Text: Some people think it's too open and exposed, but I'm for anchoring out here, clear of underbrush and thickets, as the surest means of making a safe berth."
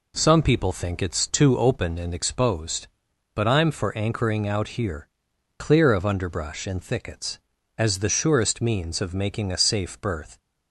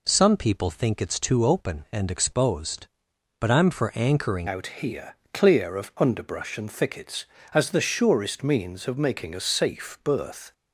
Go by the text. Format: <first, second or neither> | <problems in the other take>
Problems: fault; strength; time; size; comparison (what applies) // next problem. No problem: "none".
first | changes voice at "out"; from 4.4 s on; 6.1 s long